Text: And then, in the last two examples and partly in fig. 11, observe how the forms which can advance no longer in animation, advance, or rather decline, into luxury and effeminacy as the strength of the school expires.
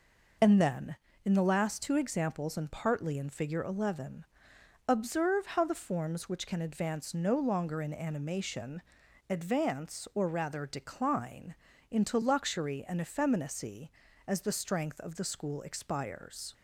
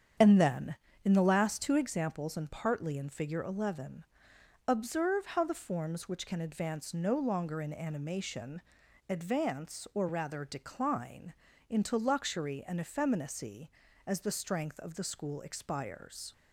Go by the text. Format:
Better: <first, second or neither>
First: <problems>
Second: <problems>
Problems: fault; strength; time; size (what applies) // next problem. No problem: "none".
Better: first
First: none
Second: starts louder than the rest; strong; until 1.9 s; 8 dB